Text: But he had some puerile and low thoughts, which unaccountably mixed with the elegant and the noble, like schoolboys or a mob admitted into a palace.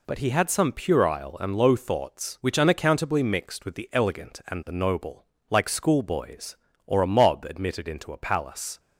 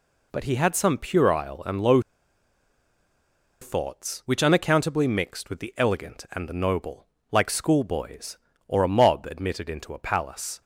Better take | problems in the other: first | pauses between "low" and "thoughts"; strong; at 1.9 s; 1.6 s long

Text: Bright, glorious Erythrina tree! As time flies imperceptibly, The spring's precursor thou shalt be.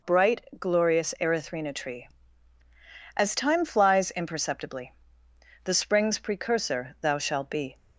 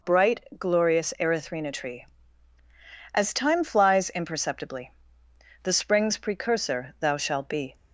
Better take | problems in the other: neither | none

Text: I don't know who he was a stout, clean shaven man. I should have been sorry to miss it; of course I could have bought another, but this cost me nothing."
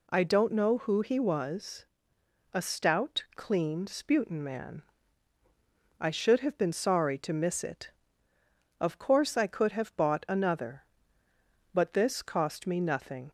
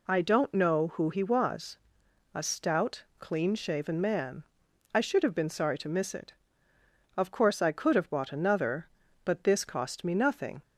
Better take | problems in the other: second | pauses between "was" and "a"; noticeable; at 1.8 s; 0.70 s long; noticeable in the second // says "sputin" for "shaven"; at 3.8 s

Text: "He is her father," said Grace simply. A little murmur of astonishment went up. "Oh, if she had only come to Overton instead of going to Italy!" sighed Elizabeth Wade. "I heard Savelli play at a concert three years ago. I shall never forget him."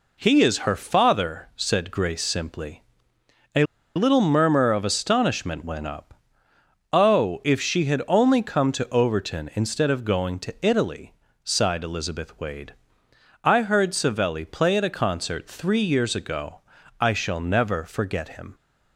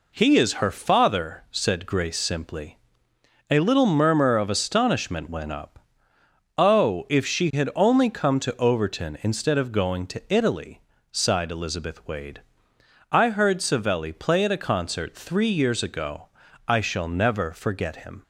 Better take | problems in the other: second | pauses between "A" and "little"; slight; at 3.6 s; 0.32 s long

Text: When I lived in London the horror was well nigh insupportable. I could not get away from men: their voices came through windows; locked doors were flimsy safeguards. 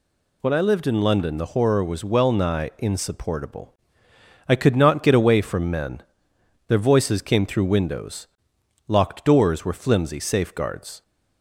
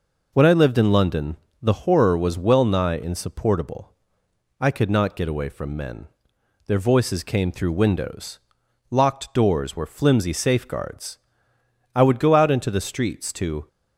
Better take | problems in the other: first | pauses between "London" and "the"; slight; at 1.3 s; 0.26 s long // goes on to say "I would go out into the streets to"; strong; from 11.9 s on; 1.7 s long

